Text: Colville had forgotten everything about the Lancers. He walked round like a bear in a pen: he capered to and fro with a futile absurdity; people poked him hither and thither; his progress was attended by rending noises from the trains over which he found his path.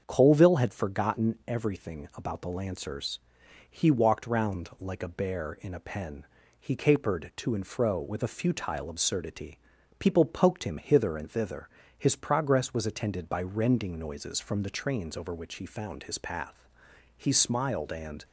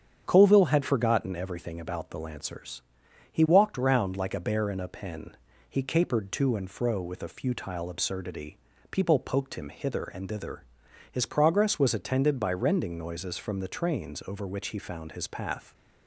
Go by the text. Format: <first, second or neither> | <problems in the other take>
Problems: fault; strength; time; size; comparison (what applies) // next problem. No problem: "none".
second | starts louder than the rest; until 1.0 s; 7 dB; strong in the second // goes on to say "He smiled and"; noticeable; from 17.1 s on; 1.1 s long